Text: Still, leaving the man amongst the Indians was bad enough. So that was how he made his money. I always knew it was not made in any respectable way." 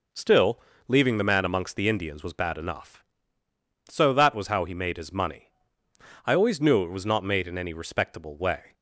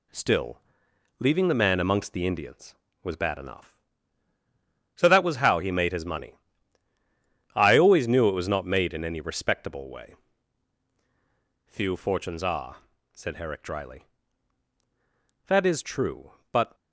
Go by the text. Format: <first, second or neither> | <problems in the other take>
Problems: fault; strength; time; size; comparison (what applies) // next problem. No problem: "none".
first | goes on to say "Few fortunes are said Herrick dryly That is true but"; strong; from 11.6 s on; 5.0 s long